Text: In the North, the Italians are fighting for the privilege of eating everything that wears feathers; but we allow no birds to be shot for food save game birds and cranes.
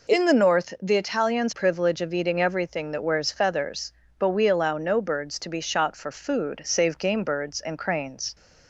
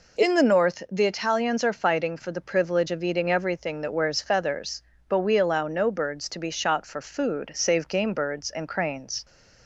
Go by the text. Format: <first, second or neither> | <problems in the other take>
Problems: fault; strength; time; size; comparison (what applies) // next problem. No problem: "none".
second | skips "are fighting for the"; at 1.5 s